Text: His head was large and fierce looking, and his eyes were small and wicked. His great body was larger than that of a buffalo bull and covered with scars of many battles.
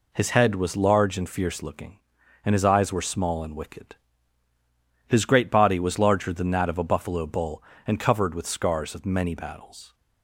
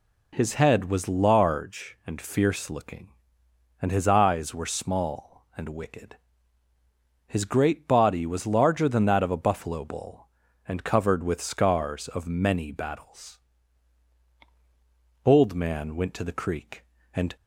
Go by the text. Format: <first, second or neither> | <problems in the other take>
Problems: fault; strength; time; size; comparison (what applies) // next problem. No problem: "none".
first | goes on to say "Old man went to the creek and"; strong; from 15.2 s on; 2.1 s long